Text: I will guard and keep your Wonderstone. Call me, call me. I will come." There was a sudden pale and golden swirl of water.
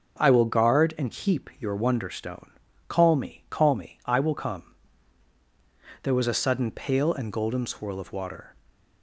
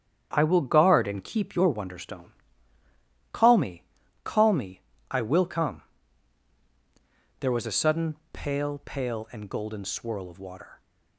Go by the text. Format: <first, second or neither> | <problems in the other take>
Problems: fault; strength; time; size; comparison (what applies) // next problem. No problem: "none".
first | starts louder than the rest; strong; until 1.3 s; 8 dB; also in the first // pauses between "sudden" and "pale"; slight; at 8.1 s; 0.16 s long // says "pale" twice; at 8.8 s